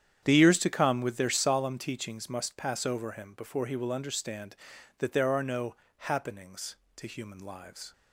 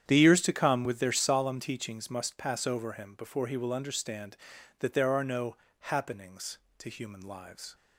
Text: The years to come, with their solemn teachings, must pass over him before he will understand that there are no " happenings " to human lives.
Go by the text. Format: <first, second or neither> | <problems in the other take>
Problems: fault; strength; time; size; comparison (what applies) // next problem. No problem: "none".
neither | starts louder than the rest; strong; the same in both